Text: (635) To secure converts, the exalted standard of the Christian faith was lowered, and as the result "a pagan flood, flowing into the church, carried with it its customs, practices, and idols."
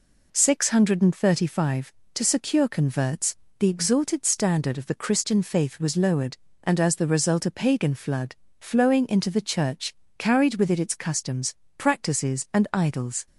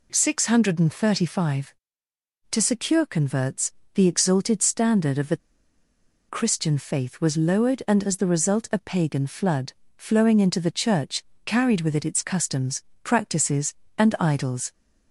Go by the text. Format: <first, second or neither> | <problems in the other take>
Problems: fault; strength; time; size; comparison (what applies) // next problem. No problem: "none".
first | pauses between "the" and "Christian"; noticeable; at 5.3 s; 0.92 s long